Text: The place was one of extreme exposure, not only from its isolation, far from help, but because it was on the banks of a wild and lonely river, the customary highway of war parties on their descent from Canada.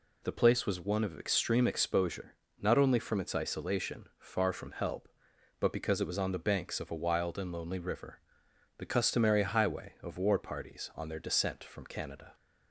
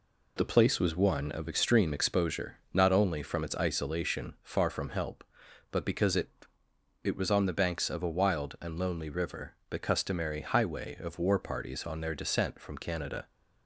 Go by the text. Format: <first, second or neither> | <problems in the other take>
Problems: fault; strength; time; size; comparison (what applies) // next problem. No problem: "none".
first | says "it" twice; at 7.0 s